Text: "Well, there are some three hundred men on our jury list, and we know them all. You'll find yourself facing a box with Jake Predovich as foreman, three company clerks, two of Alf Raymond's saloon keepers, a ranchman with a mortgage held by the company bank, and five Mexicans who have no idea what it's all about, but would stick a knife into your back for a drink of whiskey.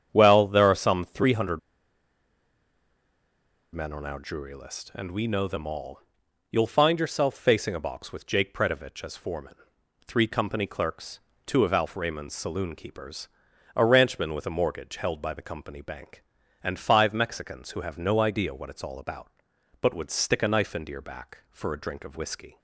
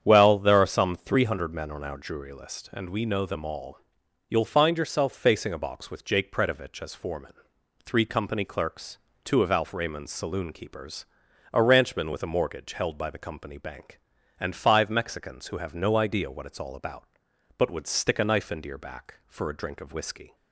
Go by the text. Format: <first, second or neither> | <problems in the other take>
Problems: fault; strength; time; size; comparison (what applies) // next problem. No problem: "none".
second | starts louder than the rest; strong; until 1.1 s; 8.5 dB; strong in the second // pauses between "hundred" and "men"; strong; at 1.5 s; 2.1 s long